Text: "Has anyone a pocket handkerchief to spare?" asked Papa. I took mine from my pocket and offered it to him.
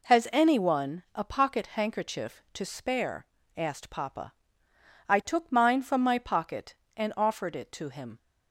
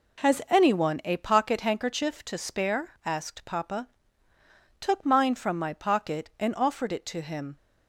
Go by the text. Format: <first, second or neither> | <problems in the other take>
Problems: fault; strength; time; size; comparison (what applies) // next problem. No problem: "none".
first | skips "I"; at 4.3 s